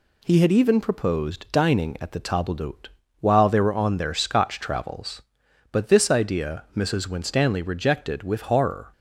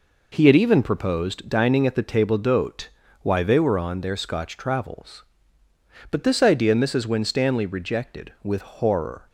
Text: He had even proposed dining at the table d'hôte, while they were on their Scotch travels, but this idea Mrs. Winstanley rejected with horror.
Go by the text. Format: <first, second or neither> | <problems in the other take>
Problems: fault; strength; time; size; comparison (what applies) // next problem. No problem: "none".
first | says "why" for "while"; at 3.2 s